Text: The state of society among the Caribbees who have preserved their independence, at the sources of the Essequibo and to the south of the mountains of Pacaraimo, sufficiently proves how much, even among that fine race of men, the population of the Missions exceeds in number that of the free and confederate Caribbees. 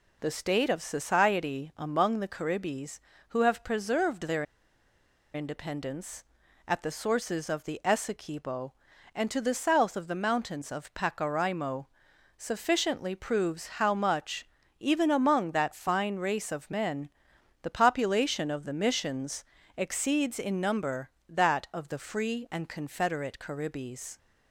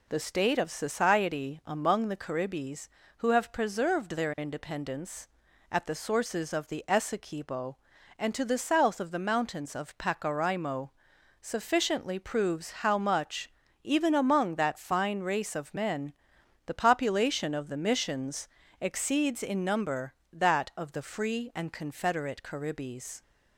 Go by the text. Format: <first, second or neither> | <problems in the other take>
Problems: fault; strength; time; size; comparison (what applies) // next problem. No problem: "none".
second | pauses between "their" and "independence"; noticeable; at 4.4 s; 0.91 s long // pauses between "Missions" and "exceeds"; slight; at 19.4 s; 0.32 s long; slight in the second